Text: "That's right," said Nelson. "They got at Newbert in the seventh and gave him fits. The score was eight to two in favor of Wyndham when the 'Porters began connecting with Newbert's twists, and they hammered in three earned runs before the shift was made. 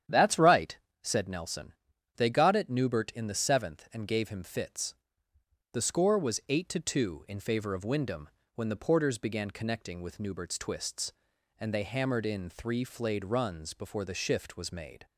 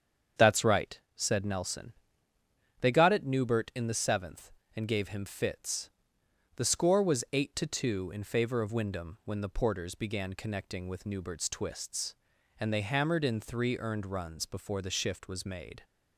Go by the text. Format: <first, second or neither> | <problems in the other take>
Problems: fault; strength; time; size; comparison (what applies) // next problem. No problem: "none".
second | starts louder than the rest; strong; until 1.3 s; 9.5 dB; strong in the second // pauses between "Wyndham" and "when"; slight; at 8.2 s; 0.26 s long // says "flayed" for "earned"; at 12.8 s